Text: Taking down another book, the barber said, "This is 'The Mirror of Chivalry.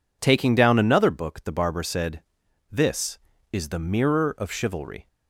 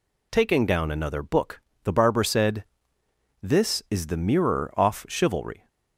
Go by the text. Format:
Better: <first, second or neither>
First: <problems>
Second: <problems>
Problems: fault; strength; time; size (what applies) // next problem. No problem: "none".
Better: first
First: none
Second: says "off" for "of"; at 4.7 s